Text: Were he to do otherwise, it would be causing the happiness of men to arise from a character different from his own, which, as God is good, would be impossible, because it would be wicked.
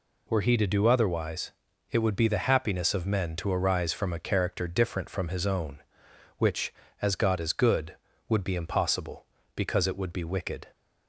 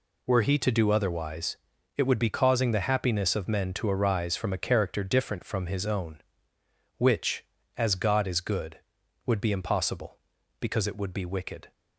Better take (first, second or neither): second